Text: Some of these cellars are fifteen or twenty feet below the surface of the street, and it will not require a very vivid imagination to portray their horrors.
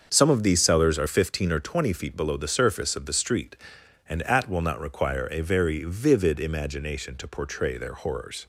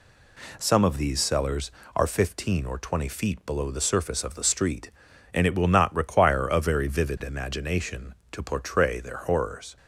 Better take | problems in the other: second | starts louder than the rest; until 1.1 s; 6.5 dB // says "at" for "it"; at 4.2 s

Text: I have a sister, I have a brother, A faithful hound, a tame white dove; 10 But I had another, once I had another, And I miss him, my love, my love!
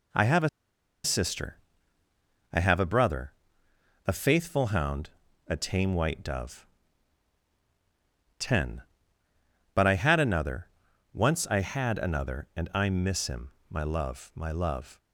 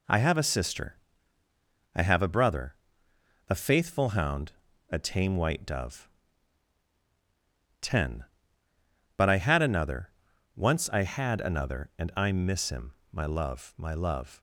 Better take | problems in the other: second | pauses between "a" and "sister"; noticeable; at 0.4 s; 0.55 s long

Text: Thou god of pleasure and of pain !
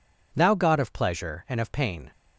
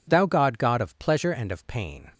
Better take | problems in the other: first | says "god" twice; at 0.5 s

